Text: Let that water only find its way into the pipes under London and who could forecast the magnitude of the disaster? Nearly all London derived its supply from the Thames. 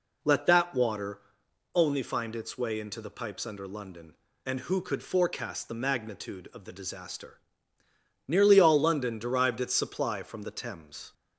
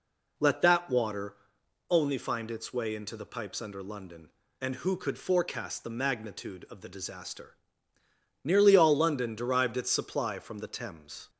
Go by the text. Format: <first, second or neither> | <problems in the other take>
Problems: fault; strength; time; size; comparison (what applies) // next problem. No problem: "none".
neither | pauses between "water" and "only"; noticeable; the same in both